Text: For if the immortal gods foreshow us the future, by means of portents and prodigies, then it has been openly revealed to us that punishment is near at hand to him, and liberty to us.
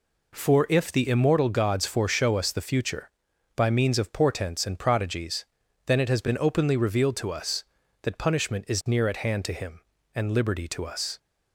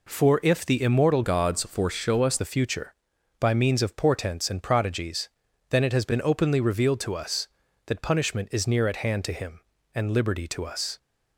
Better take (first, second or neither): first